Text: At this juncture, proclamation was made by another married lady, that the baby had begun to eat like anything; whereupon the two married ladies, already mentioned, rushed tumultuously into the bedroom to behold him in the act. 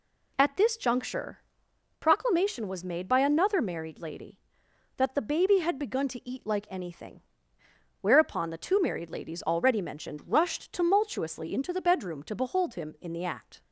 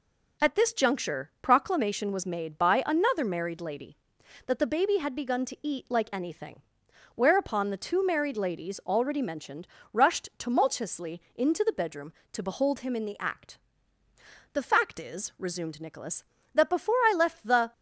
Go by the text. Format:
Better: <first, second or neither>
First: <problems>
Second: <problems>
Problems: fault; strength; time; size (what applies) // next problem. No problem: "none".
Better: first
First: none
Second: goes on to say "The fact is resumed Nicholas that before I left the"; strong; from 14.5 s on; 3.2 s long